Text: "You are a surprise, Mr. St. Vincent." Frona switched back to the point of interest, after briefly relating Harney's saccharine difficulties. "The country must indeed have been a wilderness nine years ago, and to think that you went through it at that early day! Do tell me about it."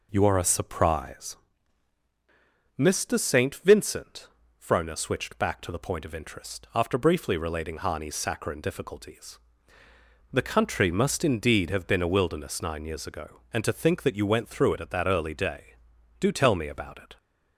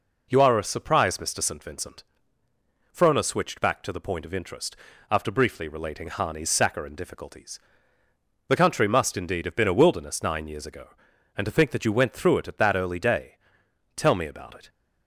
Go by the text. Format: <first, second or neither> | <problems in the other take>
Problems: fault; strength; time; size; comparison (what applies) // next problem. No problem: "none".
first | skips "Do"; at 13.6 s